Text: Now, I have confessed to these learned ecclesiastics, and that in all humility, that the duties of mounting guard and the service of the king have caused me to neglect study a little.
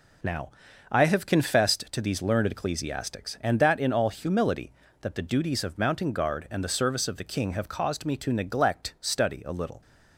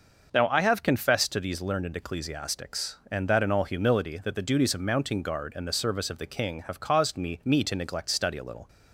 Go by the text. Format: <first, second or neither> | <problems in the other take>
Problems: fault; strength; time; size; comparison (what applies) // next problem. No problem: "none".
first | starts louder than the rest; noticeable; until 1.3 s; 6 dB // says "me" twice; at 7.4 s